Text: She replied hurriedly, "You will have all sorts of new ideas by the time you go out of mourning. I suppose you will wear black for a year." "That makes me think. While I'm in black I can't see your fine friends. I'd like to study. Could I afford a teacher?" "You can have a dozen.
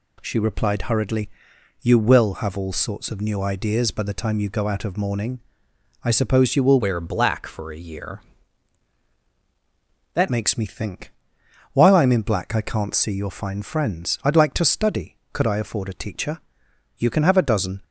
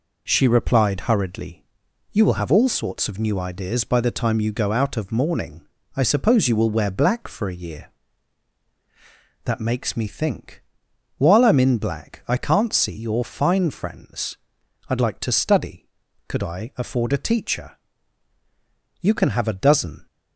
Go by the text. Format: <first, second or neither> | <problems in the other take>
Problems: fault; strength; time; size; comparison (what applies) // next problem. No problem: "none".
second | changes voice from "wear" to "That"; from 6.7 to 10.2 s; 3.5 s long